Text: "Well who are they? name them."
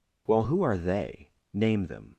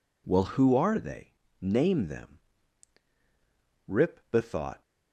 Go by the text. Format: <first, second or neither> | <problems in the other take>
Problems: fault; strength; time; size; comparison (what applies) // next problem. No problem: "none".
first | goes on to say "Rip bethought"; noticeable; from 3.8 s on; 0.94 s long